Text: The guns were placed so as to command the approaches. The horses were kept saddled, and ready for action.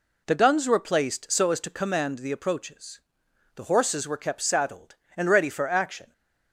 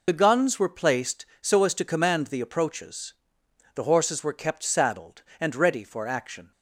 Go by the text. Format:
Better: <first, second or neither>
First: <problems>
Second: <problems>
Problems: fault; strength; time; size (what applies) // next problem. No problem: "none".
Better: first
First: none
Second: loses the start of "The"; at 0.0 s; 50 ms